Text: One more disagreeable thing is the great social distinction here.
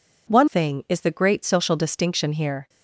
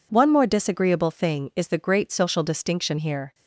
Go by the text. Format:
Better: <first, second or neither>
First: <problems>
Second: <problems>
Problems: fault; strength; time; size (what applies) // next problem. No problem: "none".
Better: second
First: skips "more disagreeable"; at 0.4 s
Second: none